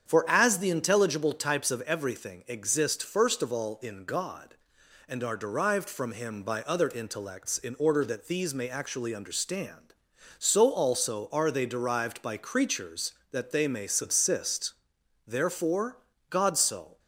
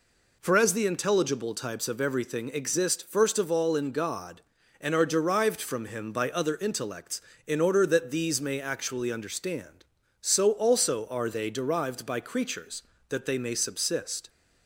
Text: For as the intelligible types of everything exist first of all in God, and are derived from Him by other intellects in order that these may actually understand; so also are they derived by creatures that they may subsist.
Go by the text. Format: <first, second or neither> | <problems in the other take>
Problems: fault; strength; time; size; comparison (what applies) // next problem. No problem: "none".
second | starts louder than the rest; strong; until 1.1 s; 7.5 dB // goes on to say "Therefore God so"; strong; from 15.2 s on; 1.7 s long